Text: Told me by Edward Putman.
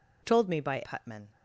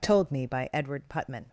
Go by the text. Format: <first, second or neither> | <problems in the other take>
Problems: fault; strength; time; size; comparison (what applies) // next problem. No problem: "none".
second | skips "Edward"; at 0.8 s